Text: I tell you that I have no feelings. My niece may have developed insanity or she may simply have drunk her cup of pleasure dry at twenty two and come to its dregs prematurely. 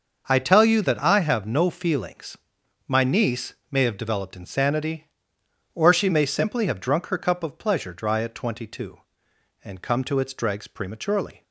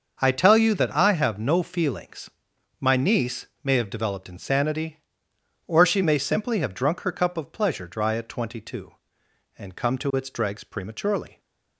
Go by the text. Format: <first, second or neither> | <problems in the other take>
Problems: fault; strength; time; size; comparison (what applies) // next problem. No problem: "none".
neither | starts louder than the rest; the same in both // pauses between "niece" and "may"; slight; the same in both